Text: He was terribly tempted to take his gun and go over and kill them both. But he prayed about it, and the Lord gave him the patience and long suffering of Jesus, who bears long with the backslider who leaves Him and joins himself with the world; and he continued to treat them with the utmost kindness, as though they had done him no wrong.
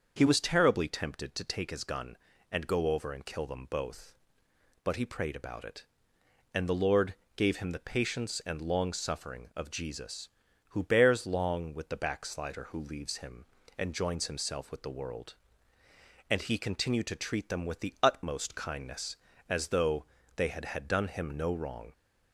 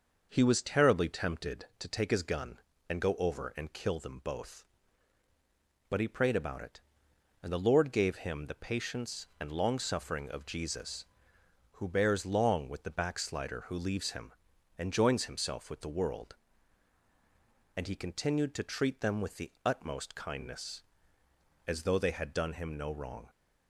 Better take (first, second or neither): second